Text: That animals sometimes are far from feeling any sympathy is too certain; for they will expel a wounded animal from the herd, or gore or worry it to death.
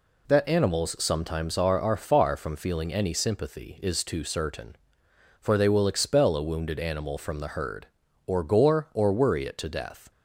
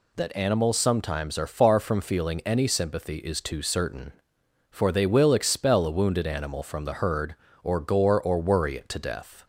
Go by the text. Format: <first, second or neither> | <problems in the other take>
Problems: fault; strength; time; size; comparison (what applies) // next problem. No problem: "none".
second | says "are" twice; at 1.8 s